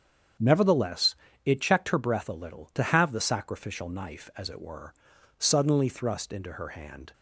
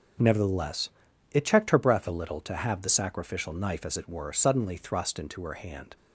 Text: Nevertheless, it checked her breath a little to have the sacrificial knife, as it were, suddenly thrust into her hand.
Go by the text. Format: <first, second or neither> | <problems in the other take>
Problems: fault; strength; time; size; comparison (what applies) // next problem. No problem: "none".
neither | starts louder than the rest; the same in both